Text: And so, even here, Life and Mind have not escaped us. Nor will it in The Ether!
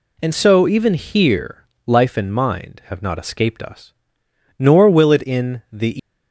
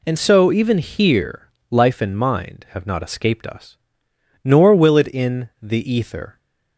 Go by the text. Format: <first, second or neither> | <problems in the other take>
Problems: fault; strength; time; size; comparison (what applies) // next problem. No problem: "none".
second | stops before "Ether"; at 5.9 s